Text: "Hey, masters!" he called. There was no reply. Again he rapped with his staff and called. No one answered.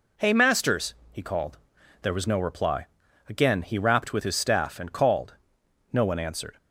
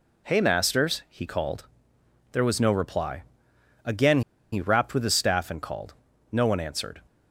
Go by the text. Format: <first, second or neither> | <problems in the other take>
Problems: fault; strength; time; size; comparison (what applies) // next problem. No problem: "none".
first | pauses between "Again" and "he"; slight; at 4.2 s; 0.31 s long